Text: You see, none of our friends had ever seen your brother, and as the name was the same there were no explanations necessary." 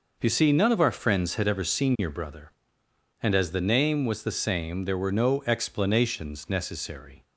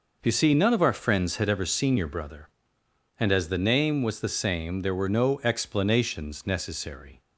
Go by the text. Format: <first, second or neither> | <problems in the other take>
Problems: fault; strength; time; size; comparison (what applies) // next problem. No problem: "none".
neither | none